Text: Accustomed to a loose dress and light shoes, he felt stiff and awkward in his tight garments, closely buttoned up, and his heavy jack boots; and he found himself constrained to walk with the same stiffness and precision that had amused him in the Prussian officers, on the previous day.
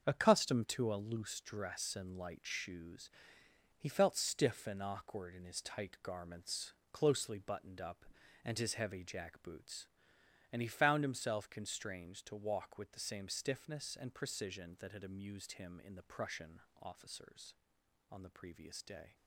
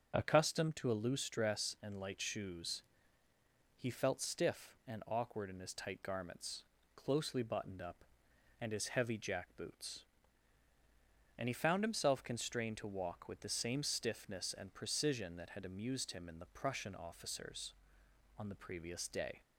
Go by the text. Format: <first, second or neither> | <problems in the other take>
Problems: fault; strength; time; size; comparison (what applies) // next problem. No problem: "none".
second | gets quieter; strong; throughout; 9 dB // starts louder than the rest; until 1.0 s; 7 dB; also in the second // pauses between "Prussian" and "officers"; slight; at 16.5 s; 0.22 s long